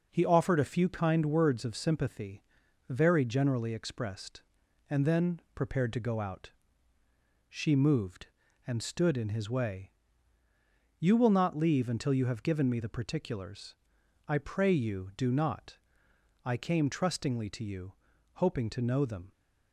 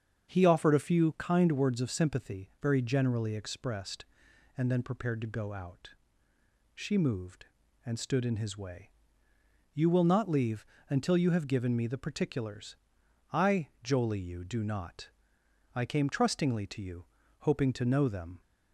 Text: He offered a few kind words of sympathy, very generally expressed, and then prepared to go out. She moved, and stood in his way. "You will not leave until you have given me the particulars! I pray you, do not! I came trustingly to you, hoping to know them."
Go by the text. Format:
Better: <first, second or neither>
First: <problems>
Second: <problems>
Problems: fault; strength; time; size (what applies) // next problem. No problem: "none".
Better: first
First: none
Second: starts louder than the rest; strong; until 1.3 s; 7 dB // pauses between "leave" and "until"; slight; at 10.6 s; 0.24 s long // says "jolie" for "pray"; at 13.8 s